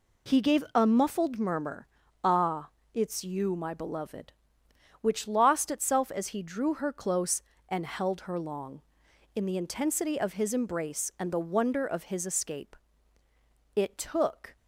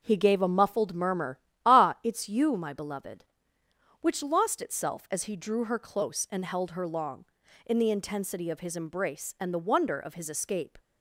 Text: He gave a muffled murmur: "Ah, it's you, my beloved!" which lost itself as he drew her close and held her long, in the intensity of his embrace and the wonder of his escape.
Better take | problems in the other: second | goes on to say "It took"; noticeable; from 13.7 s on; 0.84 s long

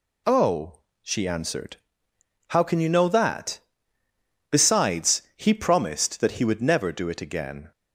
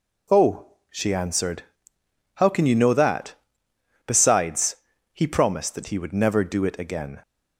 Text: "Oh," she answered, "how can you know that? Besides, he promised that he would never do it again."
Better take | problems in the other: neither | none

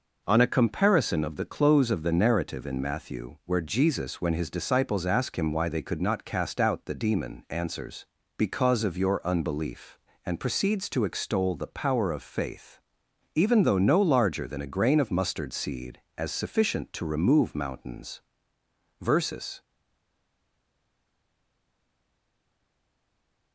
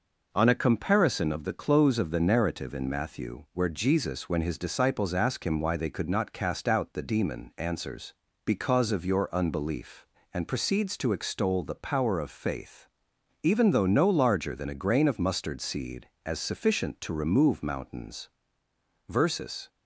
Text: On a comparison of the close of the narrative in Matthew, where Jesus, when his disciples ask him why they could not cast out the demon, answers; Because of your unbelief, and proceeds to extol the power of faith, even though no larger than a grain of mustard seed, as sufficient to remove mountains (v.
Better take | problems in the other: second | stays silent after the last word; strong; from 19.6 s on; 3.9 s long

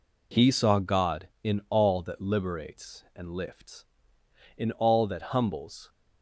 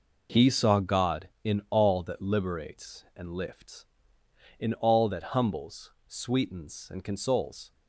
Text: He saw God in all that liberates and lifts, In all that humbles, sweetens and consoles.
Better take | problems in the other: second | stops before "sweetens and consoles"; at 5.8 s

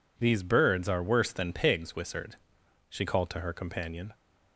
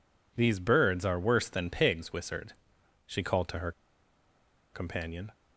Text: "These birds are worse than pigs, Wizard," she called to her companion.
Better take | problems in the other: first | pauses between "her" and "companion"; at 3.7 s; 1.0 s long

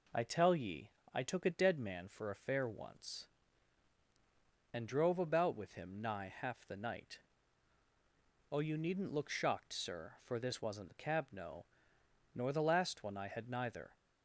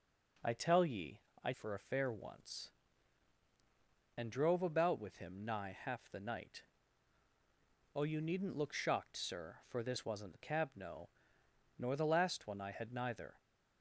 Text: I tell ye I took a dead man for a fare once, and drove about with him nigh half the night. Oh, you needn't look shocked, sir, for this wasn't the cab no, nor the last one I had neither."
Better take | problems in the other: first | pauses between "ye" and "I"; slight; at 1.1 s; 0.24 s long; slight in the first // skips "took a dead man"; at 1.5 s

